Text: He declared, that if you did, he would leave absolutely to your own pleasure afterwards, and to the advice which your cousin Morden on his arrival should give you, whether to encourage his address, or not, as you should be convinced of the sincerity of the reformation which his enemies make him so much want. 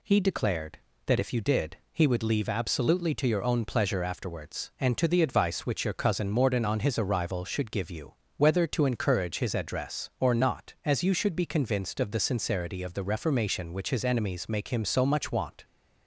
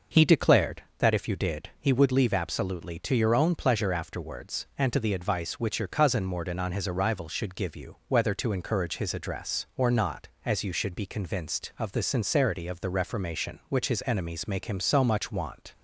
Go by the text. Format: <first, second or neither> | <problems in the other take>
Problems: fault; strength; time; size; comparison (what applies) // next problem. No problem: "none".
neither | none